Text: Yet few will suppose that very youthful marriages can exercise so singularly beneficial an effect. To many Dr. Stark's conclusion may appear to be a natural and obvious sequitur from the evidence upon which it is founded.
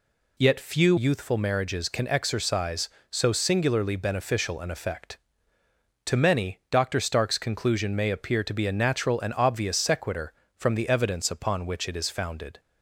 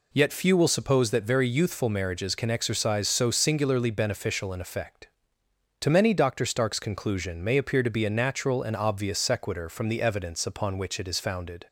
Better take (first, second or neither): second